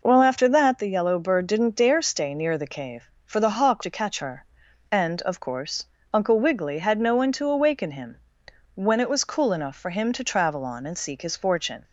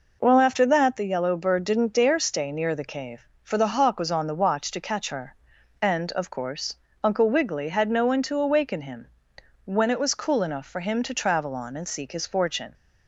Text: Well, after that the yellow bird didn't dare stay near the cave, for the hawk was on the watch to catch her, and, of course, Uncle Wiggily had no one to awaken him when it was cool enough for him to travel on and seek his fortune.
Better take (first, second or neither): second